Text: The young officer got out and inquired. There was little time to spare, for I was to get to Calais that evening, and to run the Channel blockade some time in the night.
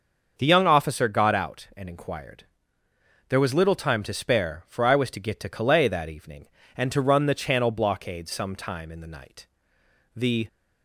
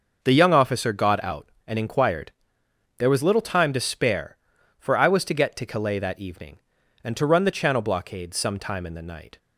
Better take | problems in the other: second | starts louder than the rest; until 1.3 s; 6.5 dB; also in the second // goes on to say "The"; slight; from 10.1 s on; 0.32 s long

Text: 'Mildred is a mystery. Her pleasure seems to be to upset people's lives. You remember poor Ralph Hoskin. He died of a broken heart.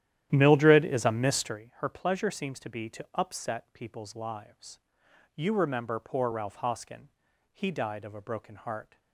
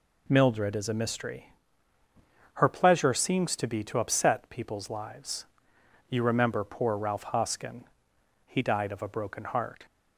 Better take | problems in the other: second | starts louder than the rest; strong; until 1.6 s; 11.5 dB

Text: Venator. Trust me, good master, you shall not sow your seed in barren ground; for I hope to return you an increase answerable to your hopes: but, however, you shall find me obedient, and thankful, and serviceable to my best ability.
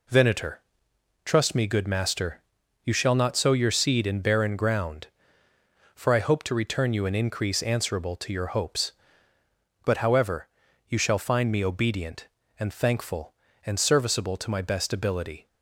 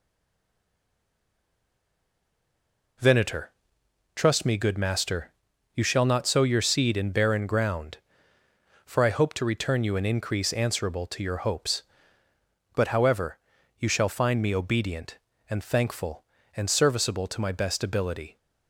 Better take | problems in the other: first | stays silent before the first word; strong; until 2.9 s; 2.9 s long

